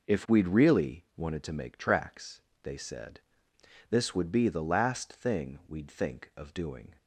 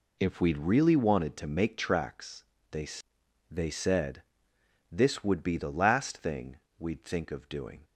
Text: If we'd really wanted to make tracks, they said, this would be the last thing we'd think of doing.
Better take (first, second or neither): first